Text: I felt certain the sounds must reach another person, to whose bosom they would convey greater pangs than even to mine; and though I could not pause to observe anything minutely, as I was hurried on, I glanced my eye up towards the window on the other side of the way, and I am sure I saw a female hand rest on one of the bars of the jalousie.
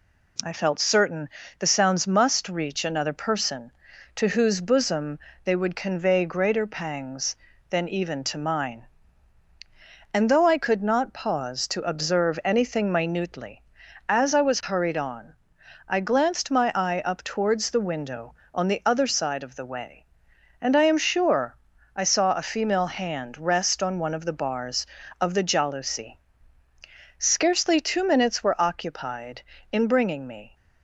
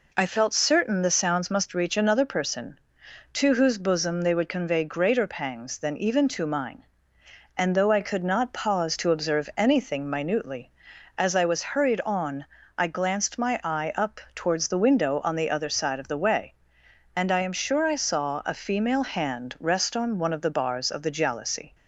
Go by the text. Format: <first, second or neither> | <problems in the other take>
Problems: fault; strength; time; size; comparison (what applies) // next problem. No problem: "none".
second | pauses between "certain" and "the"; slight; at 1.2 s; 0.32 s long // pauses between "bosom" and "they"; slight; at 5.1 s; 0.24 s long // pauses between "sure" and "I"; at 21.5 s; 0.38 s long // goes on to say "Scarcely two minutes were occupied in bringing me"; strong; from 27.2 s on; 3.3 s long